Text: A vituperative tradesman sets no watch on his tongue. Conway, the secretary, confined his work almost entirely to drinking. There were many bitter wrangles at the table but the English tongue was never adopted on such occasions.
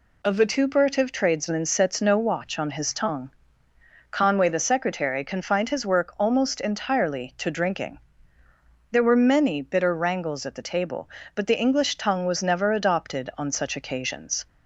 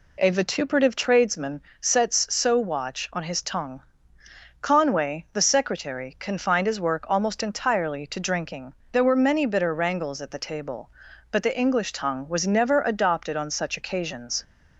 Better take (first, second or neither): first